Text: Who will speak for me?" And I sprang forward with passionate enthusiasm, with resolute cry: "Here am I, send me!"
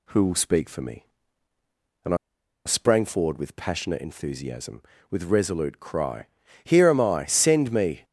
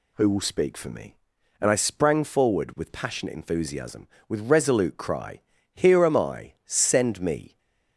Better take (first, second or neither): second